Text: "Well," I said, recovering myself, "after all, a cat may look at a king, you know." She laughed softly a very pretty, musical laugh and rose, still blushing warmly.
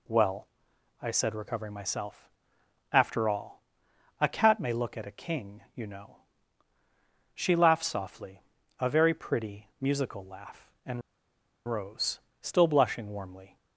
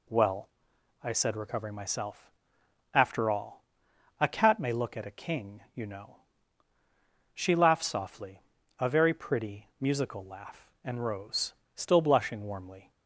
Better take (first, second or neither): second